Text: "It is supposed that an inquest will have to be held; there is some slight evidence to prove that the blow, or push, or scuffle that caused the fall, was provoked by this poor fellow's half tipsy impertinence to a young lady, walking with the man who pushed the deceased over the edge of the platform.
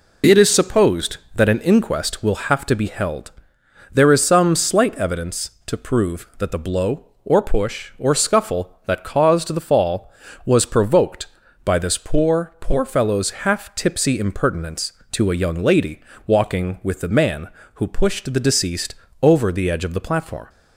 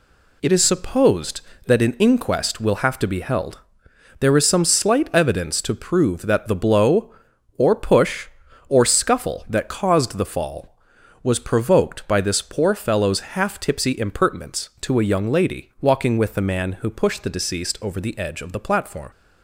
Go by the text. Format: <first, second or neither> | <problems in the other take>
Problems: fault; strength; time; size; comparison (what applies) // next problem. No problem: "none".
second | says "poor" twice; at 12.5 s // pauses between "deceased" and "over"; slight; at 18.9 s; 0.28 s long